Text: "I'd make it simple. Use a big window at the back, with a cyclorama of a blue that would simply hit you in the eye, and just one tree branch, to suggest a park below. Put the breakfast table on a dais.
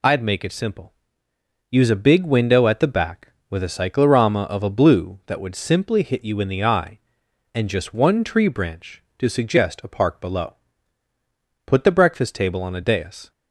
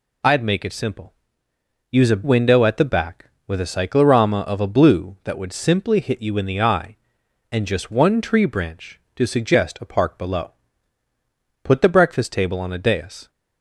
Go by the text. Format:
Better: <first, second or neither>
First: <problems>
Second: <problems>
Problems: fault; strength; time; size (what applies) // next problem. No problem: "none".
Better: first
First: none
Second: skips "big"; at 2.2 s